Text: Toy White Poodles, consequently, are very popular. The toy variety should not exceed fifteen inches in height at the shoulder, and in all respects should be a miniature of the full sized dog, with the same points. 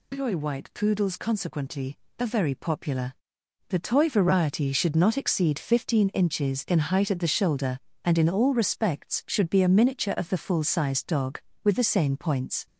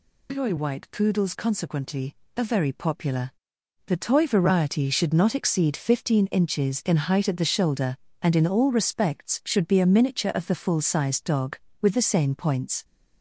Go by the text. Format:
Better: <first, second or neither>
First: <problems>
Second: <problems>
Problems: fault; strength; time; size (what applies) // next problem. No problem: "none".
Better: neither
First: none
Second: none